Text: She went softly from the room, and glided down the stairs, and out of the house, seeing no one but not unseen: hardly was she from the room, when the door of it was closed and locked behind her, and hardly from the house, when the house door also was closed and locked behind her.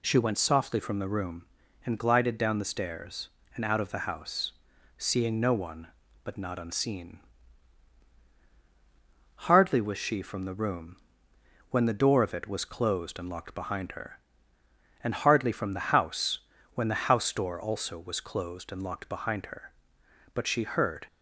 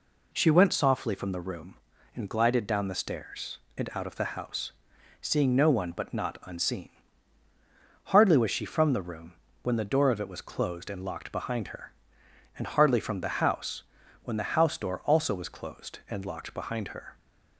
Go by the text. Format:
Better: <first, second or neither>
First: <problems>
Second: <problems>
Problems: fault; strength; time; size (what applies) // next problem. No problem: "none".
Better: second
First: goes on to say "But she heard"; noticeable; from 20.3 s on; 0.72 s long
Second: none